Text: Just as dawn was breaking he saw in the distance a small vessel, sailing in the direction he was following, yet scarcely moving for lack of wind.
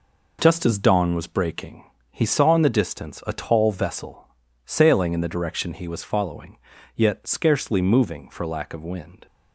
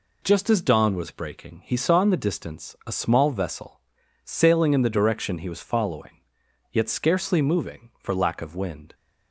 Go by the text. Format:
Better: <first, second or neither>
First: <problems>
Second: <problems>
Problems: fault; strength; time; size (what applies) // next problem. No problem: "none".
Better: second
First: pauses between "breaking" and "he"; slight; at 1.8 s; 0.28 s long // says "tall" for "small"; at 3.3 s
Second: none